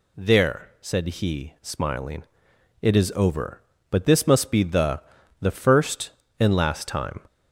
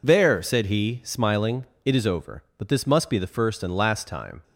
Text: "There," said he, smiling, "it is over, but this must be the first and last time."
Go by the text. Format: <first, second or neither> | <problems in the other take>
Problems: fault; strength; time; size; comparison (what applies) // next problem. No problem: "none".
second | says "the" twice; at 5.4 s